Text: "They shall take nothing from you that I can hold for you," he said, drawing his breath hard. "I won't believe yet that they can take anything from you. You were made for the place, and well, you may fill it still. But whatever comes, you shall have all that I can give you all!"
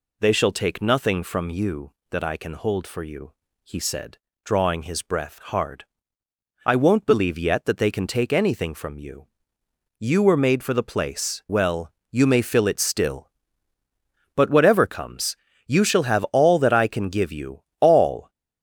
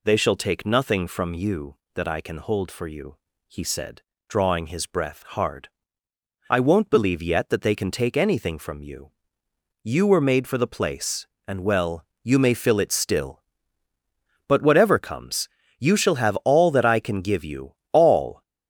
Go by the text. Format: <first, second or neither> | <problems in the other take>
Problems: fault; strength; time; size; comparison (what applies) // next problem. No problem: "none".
second | skips "and"; at 11.4 s // pauses between "you" and "all"; slight; at 17.6 s; 0.18 s long; slight in the second